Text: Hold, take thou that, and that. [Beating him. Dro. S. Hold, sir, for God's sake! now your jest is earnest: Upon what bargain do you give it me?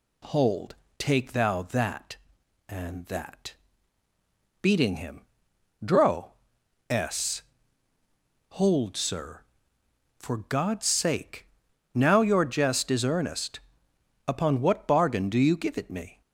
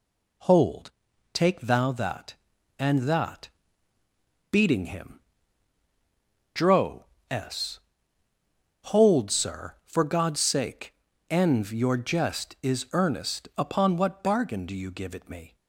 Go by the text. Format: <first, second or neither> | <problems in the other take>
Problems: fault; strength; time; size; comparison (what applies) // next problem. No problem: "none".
first | says "env" for "now"; at 11.3 s